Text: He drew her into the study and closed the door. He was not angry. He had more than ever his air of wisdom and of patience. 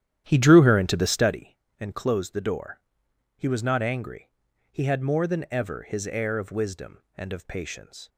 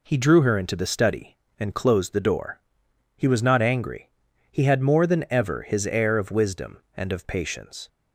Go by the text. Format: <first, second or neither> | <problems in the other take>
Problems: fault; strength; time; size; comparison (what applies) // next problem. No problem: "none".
second | starts louder than the rest; strong; until 1.4 s; 11 dB